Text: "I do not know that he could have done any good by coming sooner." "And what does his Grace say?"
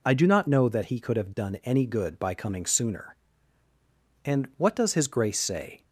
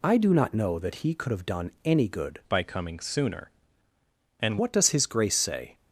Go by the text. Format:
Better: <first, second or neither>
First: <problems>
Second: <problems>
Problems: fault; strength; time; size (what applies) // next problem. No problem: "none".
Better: first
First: none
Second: pauses between "done" and "any"; slight; at 1.6 s; 0.16 s long // changes voice from "by" to "And"; from 2.4 to 4.5 s; 2.1 s long